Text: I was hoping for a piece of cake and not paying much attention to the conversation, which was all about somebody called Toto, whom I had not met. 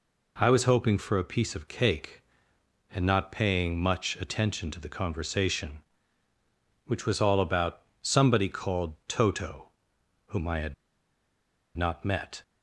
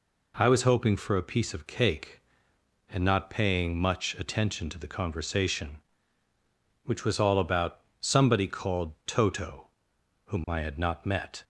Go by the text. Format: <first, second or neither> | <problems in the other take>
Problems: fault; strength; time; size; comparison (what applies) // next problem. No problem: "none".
second | pauses between "about" and "somebody"; slight; at 7.8 s; 0.22 s long; slight in the second // pauses between "had" and "not"; at 10.7 s; 1.0 s long